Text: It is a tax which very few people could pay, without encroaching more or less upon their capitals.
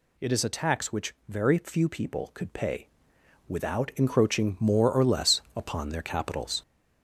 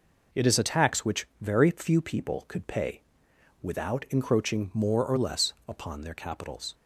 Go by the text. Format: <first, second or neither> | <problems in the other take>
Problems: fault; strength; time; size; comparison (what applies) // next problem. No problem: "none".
second | gets louder; noticeable; throughout; 4.5 dB // pauses between "which" and "very"; slight; at 1.1 s; 0.16 s long; slight in the second